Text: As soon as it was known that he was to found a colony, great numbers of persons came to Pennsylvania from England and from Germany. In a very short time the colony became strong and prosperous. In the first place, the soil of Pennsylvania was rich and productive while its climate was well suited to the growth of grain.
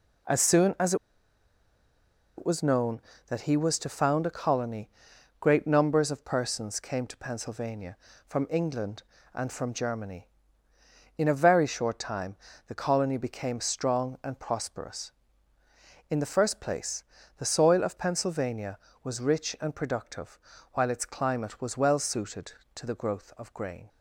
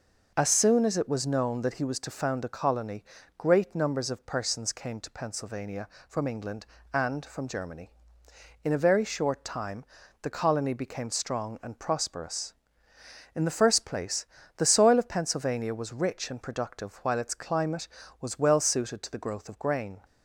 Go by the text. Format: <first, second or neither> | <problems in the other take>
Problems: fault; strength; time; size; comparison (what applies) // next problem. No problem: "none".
second | pauses between "as" and "it"; strong; at 0.9 s; 1.4 s long // pauses between "time" and "the"; slight; at 12.3 s; 0.30 s long; also in the second // pauses between "productive" and "while"; slight; at 20.3 s; 0.34 s long